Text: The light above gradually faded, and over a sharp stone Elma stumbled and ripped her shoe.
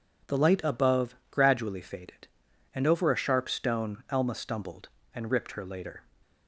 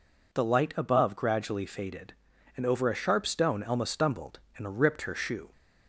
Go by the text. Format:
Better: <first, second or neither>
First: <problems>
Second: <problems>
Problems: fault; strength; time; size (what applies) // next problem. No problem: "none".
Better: second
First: pauses between "above" and "gradually"; slight; at 1.1 s; 0.16 s long // says "later" for "shoe"; at 5.6 s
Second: none